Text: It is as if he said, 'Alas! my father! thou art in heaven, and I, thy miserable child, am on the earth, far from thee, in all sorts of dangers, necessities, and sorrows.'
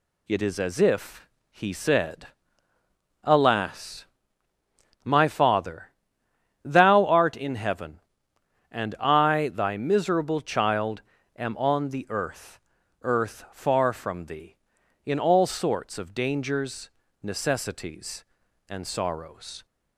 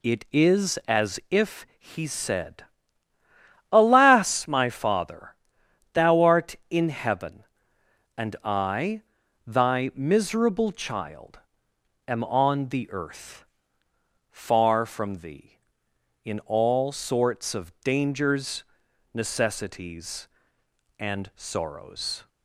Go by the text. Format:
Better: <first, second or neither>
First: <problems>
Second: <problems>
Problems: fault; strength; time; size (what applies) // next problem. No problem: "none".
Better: second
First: pauses between "if" and "he"; slight; at 1.2 s; 0.22 s long // says "earth" twice; at 13.0 s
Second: none